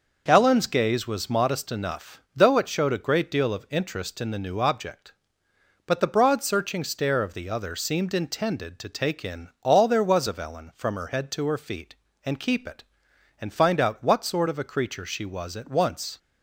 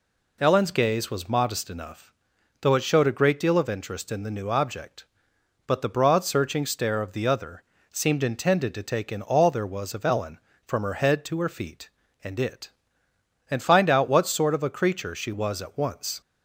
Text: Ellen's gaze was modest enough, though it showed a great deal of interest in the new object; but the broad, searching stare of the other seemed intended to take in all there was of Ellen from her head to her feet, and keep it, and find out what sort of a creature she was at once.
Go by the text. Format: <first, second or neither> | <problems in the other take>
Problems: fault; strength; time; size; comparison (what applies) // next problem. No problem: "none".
first | pauses between "other" and "seemed"; slight; at 7.6 s; 0.26 s long // skips "keep"; at 12.3 s